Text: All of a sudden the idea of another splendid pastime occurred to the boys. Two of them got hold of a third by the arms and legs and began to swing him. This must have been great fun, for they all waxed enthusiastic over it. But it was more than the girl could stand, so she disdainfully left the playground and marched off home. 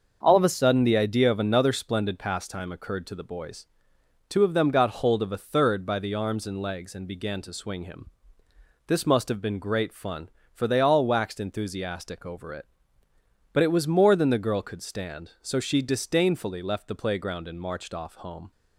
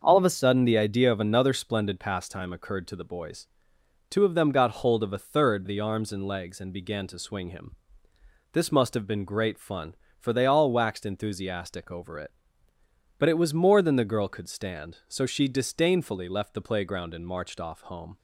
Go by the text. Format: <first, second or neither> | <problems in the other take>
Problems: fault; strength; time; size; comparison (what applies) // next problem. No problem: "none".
first | starts louder than the rest; until 1.0 s; 6.5 dB; also in the first // skips "by"; at 5.6 s